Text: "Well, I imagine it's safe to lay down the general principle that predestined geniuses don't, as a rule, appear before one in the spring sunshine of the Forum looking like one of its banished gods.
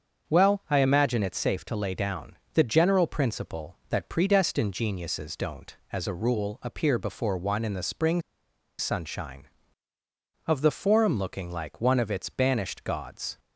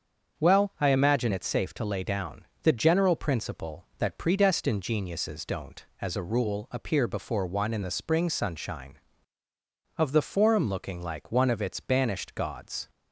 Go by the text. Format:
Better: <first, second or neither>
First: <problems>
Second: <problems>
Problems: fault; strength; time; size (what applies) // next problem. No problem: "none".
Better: second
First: starts louder than the rest; until 1.3 s; 7 dB // pauses between "down" and "the"; slight; at 2.3 s; 0.18 s long // pauses between "spring" and "sunshine"; noticeable; at 8.2 s; 0.57 s long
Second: starts louder than the rest; until 1.4 s; 7 dB // pauses between "down" and "the"; slight; at 2.4 s; 0.18 s long